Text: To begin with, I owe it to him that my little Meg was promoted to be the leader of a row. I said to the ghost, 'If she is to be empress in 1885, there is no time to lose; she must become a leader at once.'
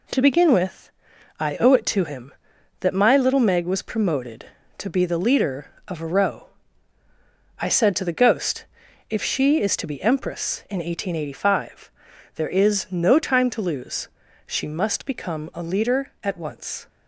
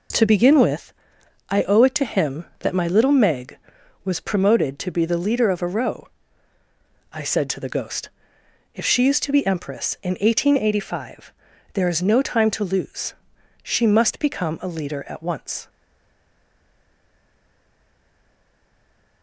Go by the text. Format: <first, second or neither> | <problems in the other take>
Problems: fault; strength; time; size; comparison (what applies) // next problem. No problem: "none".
first | stays silent after the last word; strong; from 15.6 s on; 3.6 s long